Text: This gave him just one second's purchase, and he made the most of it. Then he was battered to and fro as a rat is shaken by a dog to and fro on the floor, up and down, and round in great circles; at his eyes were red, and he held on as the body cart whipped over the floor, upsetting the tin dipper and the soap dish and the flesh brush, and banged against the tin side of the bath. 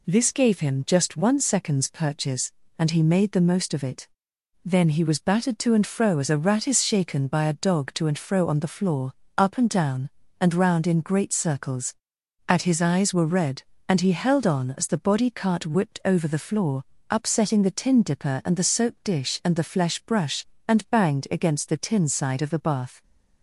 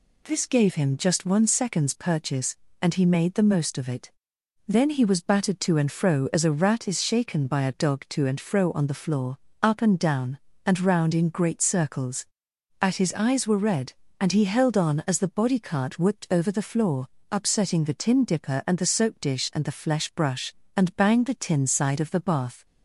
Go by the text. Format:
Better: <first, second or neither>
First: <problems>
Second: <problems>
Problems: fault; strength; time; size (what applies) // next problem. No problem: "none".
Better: first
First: none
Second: skips "against"; at 21.2 s